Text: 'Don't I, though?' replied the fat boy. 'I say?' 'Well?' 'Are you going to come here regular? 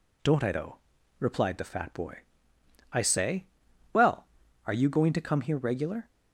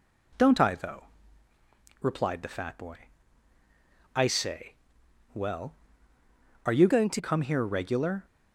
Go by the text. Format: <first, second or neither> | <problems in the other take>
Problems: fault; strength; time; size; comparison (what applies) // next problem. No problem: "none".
first | changes voice from "going" to "to"; from 6.8 to 7.2 s; 0.4 s long